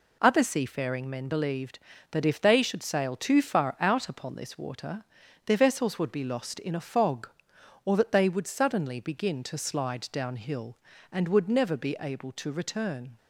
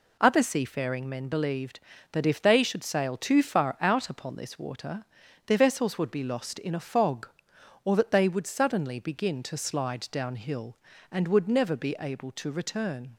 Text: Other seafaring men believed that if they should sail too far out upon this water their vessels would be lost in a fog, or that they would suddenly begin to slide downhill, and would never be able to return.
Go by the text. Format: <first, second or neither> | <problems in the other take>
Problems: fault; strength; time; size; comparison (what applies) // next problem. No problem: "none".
neither | pauses between "water" and "their"; the same in both